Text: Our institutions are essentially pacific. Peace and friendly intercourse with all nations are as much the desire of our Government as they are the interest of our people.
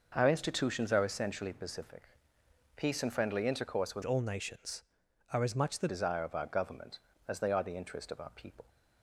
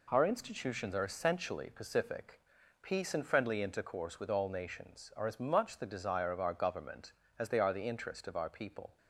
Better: second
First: changes voice from "all" to "the"; from 4.0 to 5.8 s; 1.8 s long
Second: none

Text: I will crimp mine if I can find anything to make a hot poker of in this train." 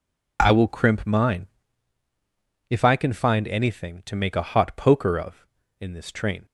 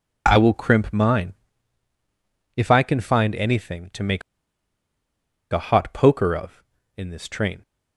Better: first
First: pauses between "mine" and "if"; at 1.4 s; 1.2 s long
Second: pauses between "mine" and "if"; at 1.3 s; 1.2 s long // pauses between "make" and "a"; strong; at 4.2 s; 1.3 s long

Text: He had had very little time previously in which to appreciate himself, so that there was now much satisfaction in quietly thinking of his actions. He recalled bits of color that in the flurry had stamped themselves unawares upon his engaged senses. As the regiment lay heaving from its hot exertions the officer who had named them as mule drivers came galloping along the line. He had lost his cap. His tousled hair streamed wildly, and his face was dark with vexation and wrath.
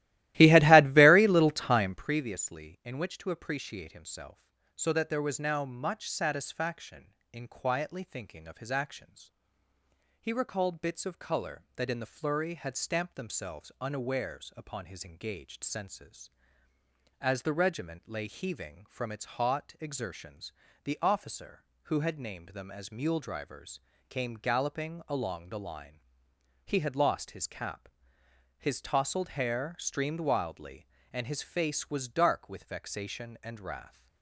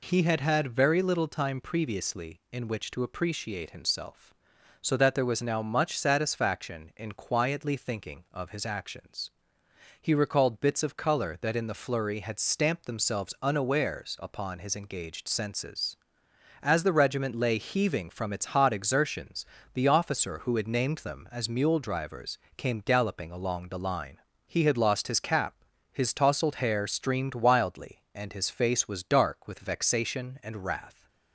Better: second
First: starts louder than the rest; strong; until 2.0 s; 16 dB // pauses between "exertions" and "the"; slight; at 20.5 s; 0.32 s long // pauses between "drivers" and "came"; slight; at 23.7 s; 0.30 s long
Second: pauses between "exertions" and "the"; slight; at 19.4 s; 0.26 s long // pauses between "drivers" and "came"; slight; at 22.3 s; 0.20 s long

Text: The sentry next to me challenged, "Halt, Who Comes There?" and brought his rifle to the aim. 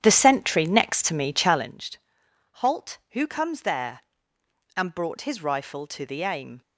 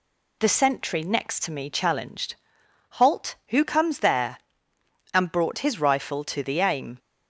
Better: second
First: starts louder than the rest; strong; until 1.8 s; 10 dB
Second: none

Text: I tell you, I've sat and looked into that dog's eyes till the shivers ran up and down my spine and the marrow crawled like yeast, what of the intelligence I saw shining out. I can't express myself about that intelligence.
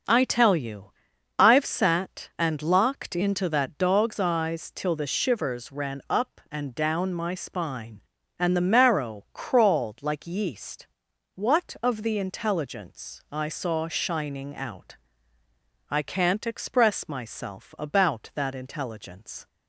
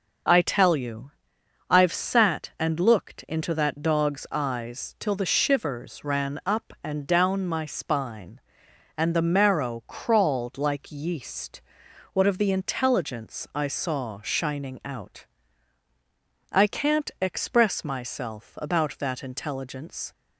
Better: second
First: starts louder than the rest; until 1.5 s; 6.5 dB // says "locked" for "looked"; at 2.6 s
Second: none

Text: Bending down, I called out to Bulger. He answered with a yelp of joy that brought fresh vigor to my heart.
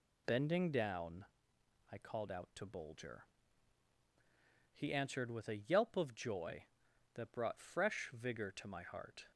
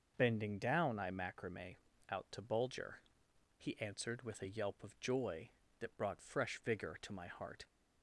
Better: first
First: none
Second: starts louder than the rest; noticeable; until 1.1 s; 6 dB // says "macrame" for "called"; at 1.0 s

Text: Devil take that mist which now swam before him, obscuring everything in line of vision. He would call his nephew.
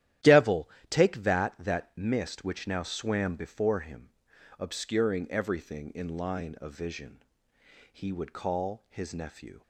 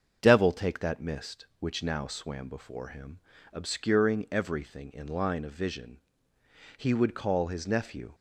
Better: second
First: starts louder than the rest; strong; until 1.4 s; 12 dB // pauses between "Devil" and "take"; slight; at 0.6 s; 0.22 s long // says "that" twice; at 1.5 s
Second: starts louder than the rest; until 1.2 s; 7 dB

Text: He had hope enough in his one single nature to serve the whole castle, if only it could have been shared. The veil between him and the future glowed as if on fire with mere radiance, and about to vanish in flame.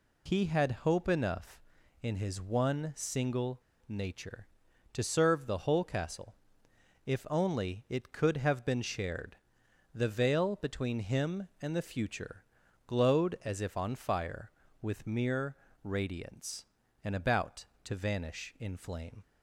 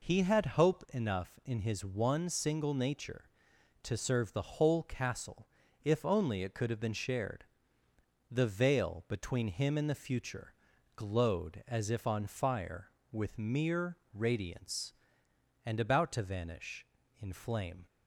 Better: second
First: pauses between "single" and "nature"; slight; at 3.6 s; 0.28 s long // pauses between "future" and "glowed"; at 12.4 s; 0.42 s long // pauses between "mere" and "radiance"; slight; at 15.5 s; 0.26 s long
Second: pauses between "future" and "glowed"; at 10.5 s; 0.42 s long // pauses between "mere" and "radiance"; slight; at 13.9 s; 0.16 s long

